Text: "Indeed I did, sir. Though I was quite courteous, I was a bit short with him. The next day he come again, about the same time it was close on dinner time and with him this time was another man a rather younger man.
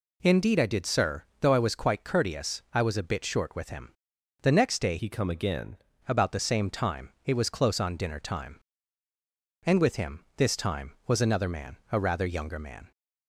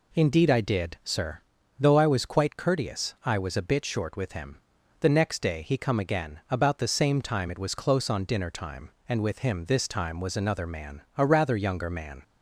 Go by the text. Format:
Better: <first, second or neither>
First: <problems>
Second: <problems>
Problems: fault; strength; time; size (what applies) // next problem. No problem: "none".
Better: second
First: changes voice from "he" to "again"; from 4.9 to 5.7 s; 0.8 s long // pauses between "man" and "a"; slight; at 11.7 s; 0.16 s long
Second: none